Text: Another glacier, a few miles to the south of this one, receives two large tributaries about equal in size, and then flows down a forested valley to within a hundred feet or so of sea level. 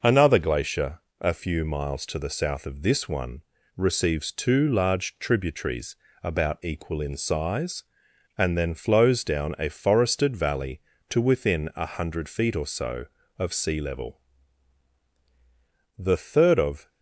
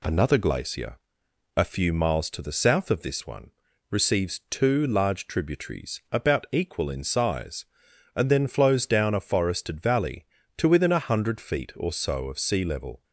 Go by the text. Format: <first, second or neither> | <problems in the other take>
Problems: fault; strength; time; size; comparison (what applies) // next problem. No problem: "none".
second | pauses between "tributaries" and "about"; slight; at 5.9 s; 0.26 s long // goes on to say "The third of"; noticeable; from 15.9 s on; 0.90 s long